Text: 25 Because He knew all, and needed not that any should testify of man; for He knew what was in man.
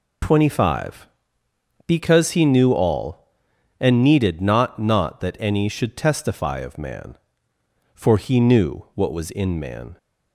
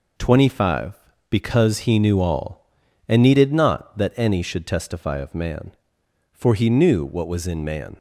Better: second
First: says "not" twice; at 4.7 s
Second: none

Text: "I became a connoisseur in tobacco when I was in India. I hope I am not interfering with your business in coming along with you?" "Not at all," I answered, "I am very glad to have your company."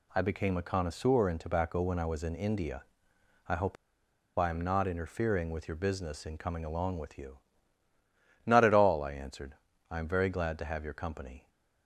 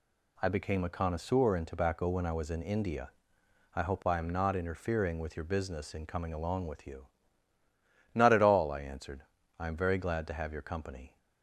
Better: second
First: pauses between "hope" and "I"; noticeable; at 3.7 s; 0.63 s long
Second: none

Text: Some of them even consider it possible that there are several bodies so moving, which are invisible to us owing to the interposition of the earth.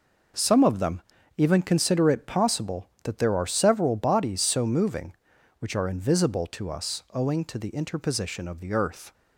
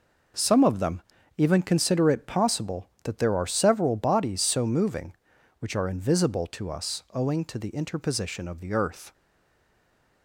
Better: first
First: pauses between "them" and "even"; slight; at 1.0 s; 0.36 s long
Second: pauses between "them" and "even"; slight; at 1.0 s; 0.36 s long // stays silent after the last word; from 9.1 s on; 1.1 s long

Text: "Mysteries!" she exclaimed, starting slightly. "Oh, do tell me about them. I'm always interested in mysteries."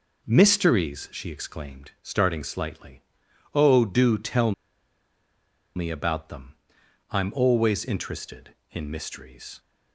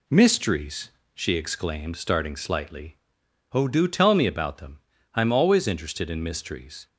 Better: second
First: pauses between "tell" and "me"; at 4.5 s; 1.2 s long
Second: none

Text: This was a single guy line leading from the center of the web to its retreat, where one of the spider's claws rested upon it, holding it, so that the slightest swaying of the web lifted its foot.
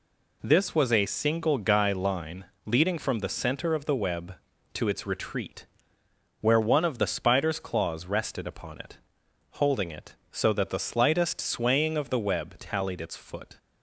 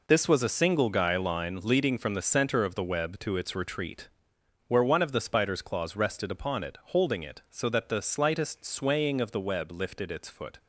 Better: second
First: pauses between "line" and "leading"; slight; at 2.4 s; 0.20 s long // says "tallied" for "lifted"; at 12.5 s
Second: none

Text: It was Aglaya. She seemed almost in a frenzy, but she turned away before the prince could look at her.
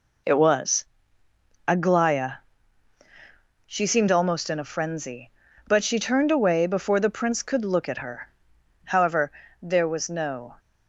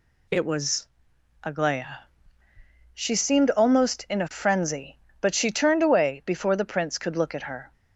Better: second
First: pauses between "was" and "Aglaya"; noticeable; at 0.8 s; 0.82 s long // goes on to say "However there was no"; strong; from 8.8 s on; 1.6 s long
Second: pauses between "was" and "Aglaya"; noticeable; at 0.8 s; 0.56 s long

